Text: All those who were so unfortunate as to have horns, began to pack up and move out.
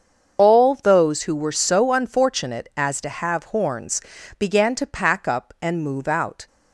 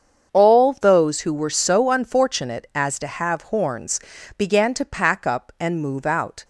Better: second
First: loses the start of "All"; at 0.3 s; 65 ms // starts louder than the rest; until 1.4 s; 6.5 dB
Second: starts louder than the rest; until 1.3 s; 7 dB

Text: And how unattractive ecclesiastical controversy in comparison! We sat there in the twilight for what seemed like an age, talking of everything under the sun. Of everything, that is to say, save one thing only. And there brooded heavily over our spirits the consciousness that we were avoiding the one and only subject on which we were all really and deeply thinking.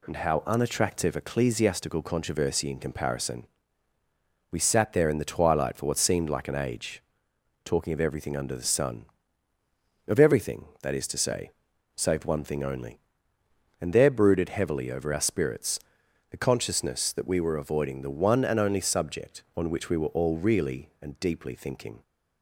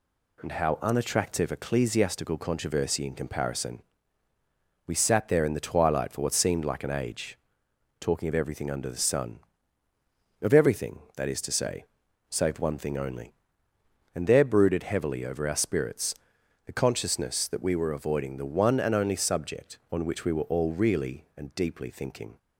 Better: neither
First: pauses between "spirits" and "the"; noticeable; at 15.7 s; 0.52 s long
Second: pauses between "spirits" and "the"; noticeable; at 16.1 s; 0.52 s long

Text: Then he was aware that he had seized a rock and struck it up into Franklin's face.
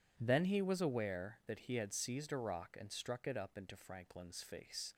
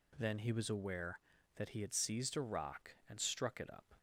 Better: first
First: none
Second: stops before "into Franklin's face"; at 3.9 s

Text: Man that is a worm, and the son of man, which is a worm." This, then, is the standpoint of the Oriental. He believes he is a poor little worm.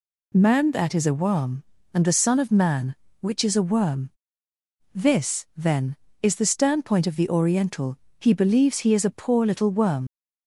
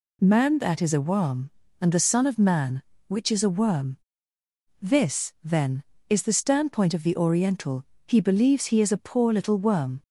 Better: second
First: leaves "worm" unfinished; at 10.0 s; 80 ms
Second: none

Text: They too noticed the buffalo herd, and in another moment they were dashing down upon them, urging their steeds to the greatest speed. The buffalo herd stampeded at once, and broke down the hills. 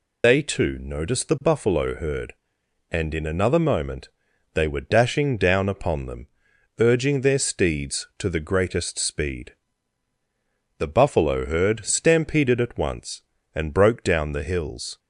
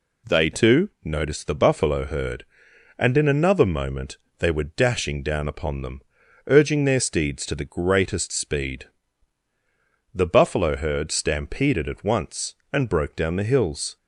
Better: second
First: loses the start of "They"; at 0.2 s; 145 ms // pauses between "moment" and "they"; noticeable; at 4.0 s; 0.46 s long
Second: pauses between "moment" and "they"; slight; at 4.1 s; 0.20 s long

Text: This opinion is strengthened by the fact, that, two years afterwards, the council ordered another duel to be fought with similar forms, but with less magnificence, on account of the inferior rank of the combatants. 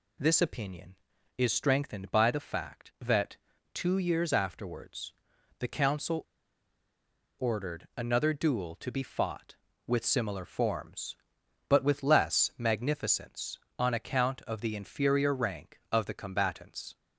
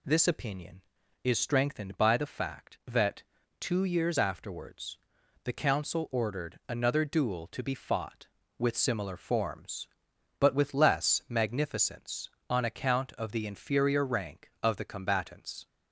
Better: second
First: pauses between "council" and "ordered"; at 6.2 s; 1.1 s long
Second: none

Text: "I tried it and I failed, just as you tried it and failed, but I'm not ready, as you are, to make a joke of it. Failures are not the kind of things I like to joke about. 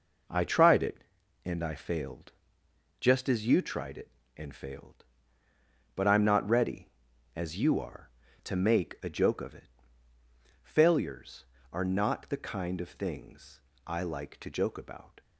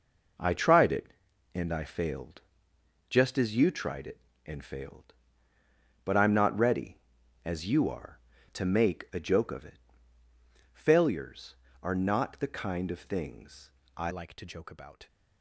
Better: first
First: pauses between "things" and "I"; slight; at 13.6 s; 0.26 s long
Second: pauses between "things" and "I"; slight; at 13.7 s; 0.26 s long // changes voice at "like"; from 14.0 s on; 1.0 s long

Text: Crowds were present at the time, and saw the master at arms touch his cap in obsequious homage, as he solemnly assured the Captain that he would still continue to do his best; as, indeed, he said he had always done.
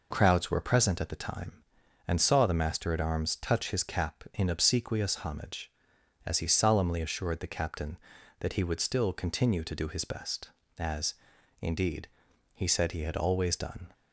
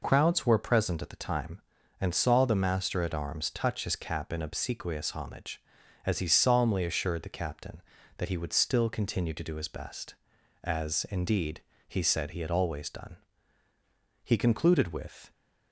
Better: first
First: none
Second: goes on to say "He concluded with"; noticeable; from 14.2 s on; 1.0 s long

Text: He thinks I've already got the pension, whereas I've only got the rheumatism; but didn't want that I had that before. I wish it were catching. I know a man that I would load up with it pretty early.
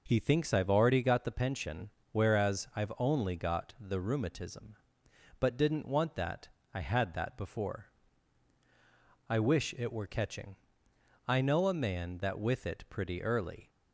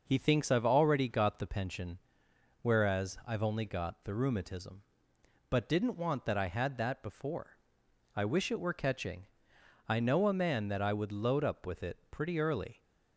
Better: second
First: pauses between "that" and "I"; slight; at 6.4 s; 0.26 s long // skips "I would load up"; at 12.3 s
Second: none

